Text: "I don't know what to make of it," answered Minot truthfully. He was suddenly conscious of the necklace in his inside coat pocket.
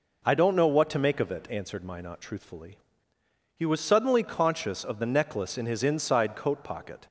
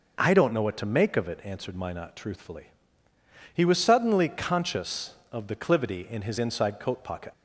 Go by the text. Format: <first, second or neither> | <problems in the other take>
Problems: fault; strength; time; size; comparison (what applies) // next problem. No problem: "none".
first | says "clivity" for "necklace"; at 5.5 s